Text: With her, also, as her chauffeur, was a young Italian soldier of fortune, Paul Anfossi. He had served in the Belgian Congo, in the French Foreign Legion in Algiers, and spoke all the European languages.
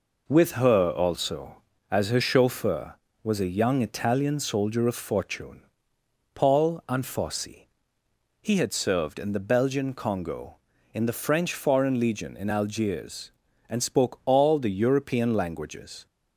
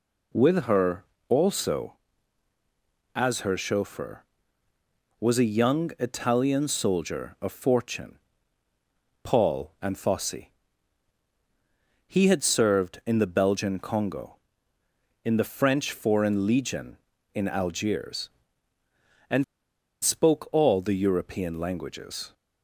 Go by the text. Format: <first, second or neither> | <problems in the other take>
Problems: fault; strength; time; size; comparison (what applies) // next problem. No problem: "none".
first | pauses between "and" and "spoke"; noticeable; at 19.4 s; 0.58 s long